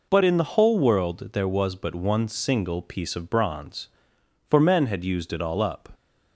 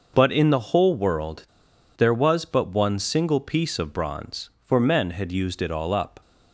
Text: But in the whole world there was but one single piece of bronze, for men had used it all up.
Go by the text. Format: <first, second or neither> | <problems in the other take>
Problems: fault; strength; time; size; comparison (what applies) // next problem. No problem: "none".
first | pauses between "world" and "there"; noticeable; at 1.4 s; 0.51 s long